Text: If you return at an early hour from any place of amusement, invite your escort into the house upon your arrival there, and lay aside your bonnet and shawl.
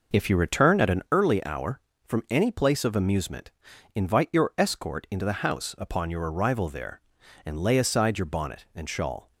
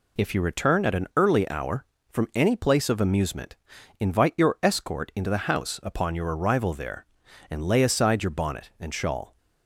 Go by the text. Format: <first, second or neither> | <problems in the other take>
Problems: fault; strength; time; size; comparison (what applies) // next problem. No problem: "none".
second | starts louder than the rest; noticeable; until 1.2 s; 5.5 dB